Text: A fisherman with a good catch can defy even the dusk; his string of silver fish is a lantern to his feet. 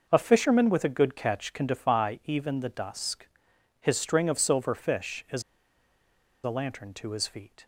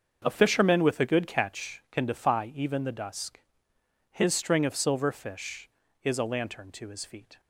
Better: second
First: starts louder than the rest; noticeable; until 1.1 s; 6 dB // pauses between "is" and "a"; at 5.4 s; 1.0 s long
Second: starts louder than the rest; until 1.2 s; 7 dB

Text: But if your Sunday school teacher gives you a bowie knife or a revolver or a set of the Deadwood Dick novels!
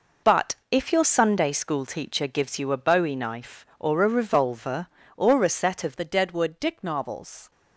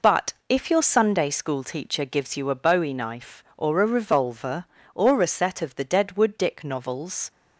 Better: second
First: changes voice at "the"; from 5.9 s on; 1.6 s long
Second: none

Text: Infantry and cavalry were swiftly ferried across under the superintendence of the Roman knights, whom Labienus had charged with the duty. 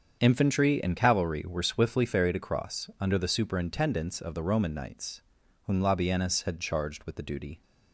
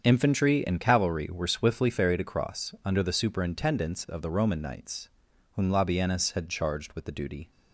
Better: neither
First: starts louder than the rest; strong; until 1.2 s; 7.5 dB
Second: starts louder than the rest; strong; until 1.0 s; 7 dB

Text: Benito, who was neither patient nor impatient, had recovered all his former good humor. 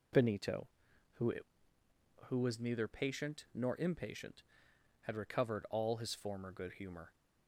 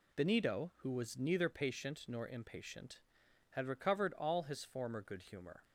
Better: second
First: says "who" twice; at 2.2 s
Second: none

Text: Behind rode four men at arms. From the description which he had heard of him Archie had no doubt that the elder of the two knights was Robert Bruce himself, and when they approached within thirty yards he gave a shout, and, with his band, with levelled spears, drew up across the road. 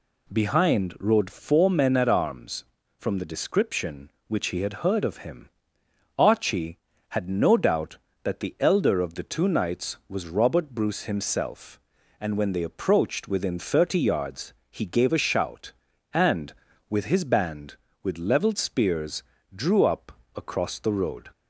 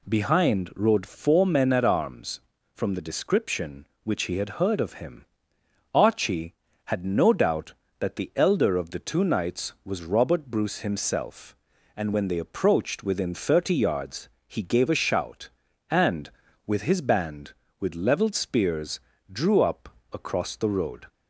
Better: neither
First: pauses between "him" and "Archie"; noticeable; at 5.4 s; 0.68 s long // pauses between "yards" and "he"; slight; at 14.5 s; 0.18 s long // pauses between "up" and "across"; slight; at 20.1 s; 0.22 s long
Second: pauses between "him" and "Archie"; noticeable; at 5.2 s; 0.68 s long // pauses between "yards" and "he"; slight; at 14.2 s; 0.20 s long // pauses between "up" and "across"; slight; at 19.8 s; 0.22 s long

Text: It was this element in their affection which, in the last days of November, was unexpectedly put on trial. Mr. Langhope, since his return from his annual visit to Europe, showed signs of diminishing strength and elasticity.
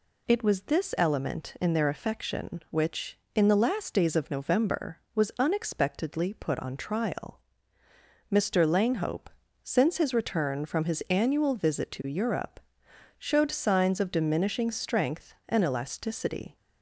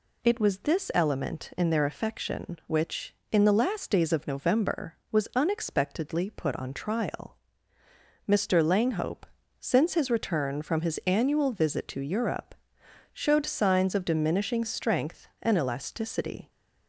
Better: neither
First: none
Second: none

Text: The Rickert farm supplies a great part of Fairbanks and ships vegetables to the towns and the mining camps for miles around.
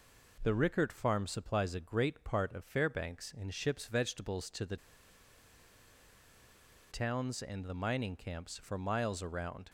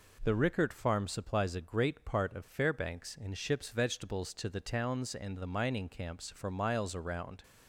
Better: second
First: pauses between "the" and "towns"; strong; at 4.7 s; 2.1 s long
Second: none

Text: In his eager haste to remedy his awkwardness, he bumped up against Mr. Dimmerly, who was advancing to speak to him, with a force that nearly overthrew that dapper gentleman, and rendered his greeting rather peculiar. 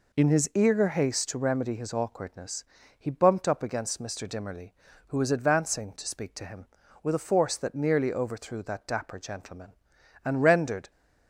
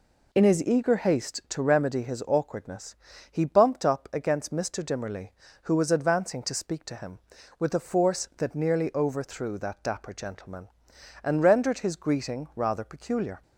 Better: second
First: stops before "his greeting rather peculiar"; at 10.8 s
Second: none

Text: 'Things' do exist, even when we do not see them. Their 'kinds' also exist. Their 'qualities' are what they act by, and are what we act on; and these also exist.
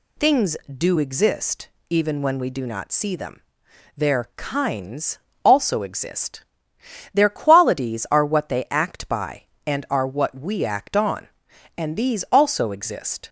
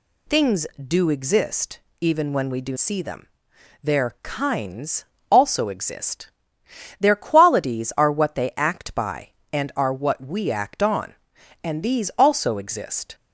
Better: first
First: pauses between "kinds" and "also"; slight; at 5.1 s; 0.26 s long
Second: skips "not"; at 2.7 s // pauses between "kinds" and "also"; slight; at 5.0 s; 0.26 s long

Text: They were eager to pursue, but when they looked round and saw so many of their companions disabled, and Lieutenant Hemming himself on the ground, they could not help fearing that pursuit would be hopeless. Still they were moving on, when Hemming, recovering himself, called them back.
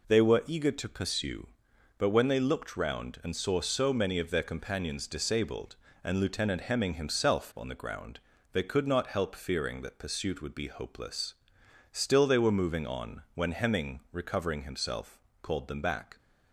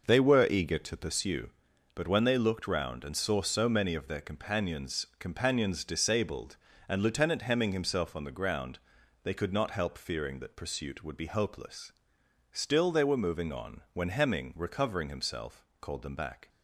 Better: first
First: none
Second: says "companions" twice; at 5.1 s

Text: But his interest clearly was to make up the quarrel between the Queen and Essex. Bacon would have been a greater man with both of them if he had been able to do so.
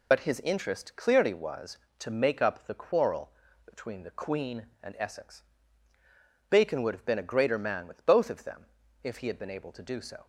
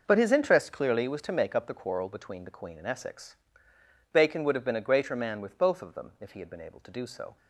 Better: second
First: loses the start of "But"; at 0.1 s; 50 ms // pauses between "quarrel" and "between"; slight; at 3.3 s; 0.32 s long // pauses between "them" and "if"; slight; at 8.6 s; 0.36 s long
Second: none

